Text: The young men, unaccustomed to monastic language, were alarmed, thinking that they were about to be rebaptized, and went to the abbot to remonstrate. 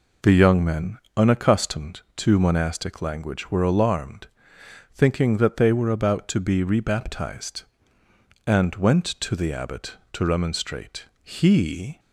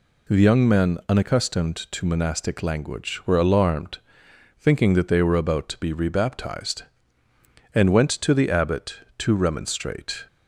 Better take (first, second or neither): second